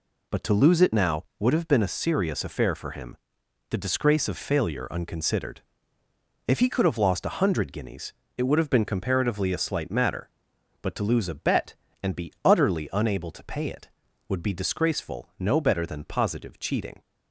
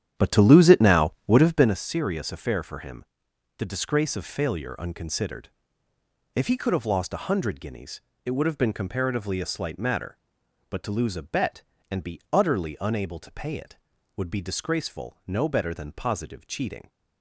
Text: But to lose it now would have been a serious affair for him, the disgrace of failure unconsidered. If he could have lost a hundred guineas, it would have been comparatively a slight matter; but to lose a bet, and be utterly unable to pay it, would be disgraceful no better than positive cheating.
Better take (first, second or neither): first